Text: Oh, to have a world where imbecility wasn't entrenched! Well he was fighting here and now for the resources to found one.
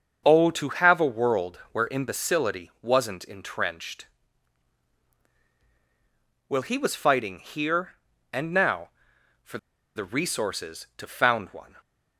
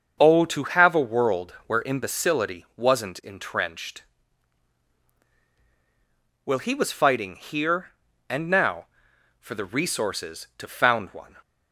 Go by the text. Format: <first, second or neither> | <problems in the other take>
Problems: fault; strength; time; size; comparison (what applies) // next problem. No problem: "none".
second | starts louder than the rest; until 1.2 s; 6.5 dB; also in the second // pauses between "for" and "the"; at 9.5 s; 0.38 s long